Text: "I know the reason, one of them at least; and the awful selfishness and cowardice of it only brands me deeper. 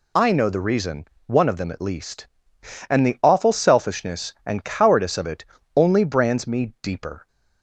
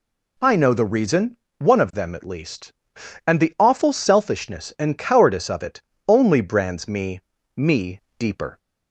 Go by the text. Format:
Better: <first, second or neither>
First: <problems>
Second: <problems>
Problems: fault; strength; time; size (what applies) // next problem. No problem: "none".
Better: first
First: pauses between "it" and "only"; slight; at 5.4 s; 0.32 s long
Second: pauses between "it" and "only"; slight; at 5.8 s; 0.26 s long // says "me" twice; at 7.5 s